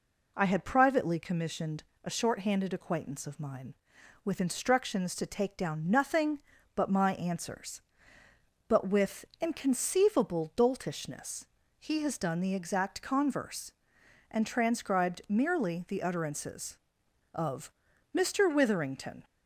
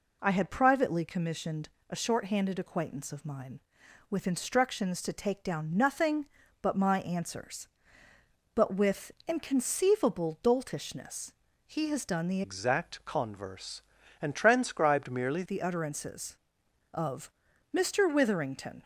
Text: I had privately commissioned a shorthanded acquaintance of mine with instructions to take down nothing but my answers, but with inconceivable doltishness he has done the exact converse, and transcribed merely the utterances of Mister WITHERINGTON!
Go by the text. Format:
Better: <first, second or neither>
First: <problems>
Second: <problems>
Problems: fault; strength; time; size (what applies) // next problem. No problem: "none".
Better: first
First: pauses between "commissioned" and "a"; slight; at 1.8 s; 0.20 s long // pauses between "with" and "inconceivable"; slight; at 9.2 s; 0.16 s long // pauses between "doltishness" and "he"; slight; at 11.4 s; 0.33 s long // pauses between "of" and "Mister"; at 17.7 s; 0.40 s long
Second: pauses between "commissioned" and "a"; slight; at 1.6 s; 0.20 s long // pauses between "with" and "inconceivable"; slight; at 9.1 s; 0.16 s long // pauses between "doltishness" and "he"; slight; at 11.3 s; 0.34 s long // changes voice from "exact" to "merely"; from 12.4 to 15.4 s; 3.0 s long // pauses between "of" and "Mister"; at 17.3 s; 0.40 s long